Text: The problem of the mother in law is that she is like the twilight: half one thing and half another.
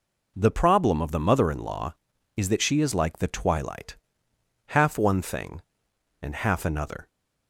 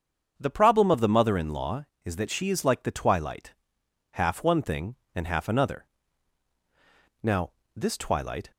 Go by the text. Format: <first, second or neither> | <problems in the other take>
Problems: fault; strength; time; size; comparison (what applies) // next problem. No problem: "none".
first | starts louder than the rest; until 1.4 s; 7 dB // goes on to say "Now this twilight"; noticeable; from 7.2 s on; 1.2 s long